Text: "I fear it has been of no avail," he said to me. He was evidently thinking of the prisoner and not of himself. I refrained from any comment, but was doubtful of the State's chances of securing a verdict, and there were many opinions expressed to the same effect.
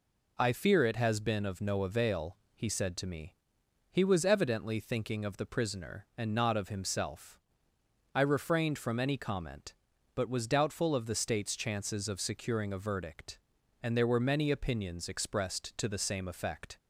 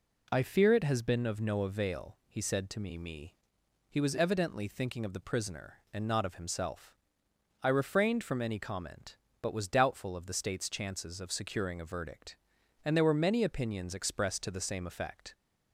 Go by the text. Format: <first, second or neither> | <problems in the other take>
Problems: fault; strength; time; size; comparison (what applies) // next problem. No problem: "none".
first | says "me" twice; at 2.9 s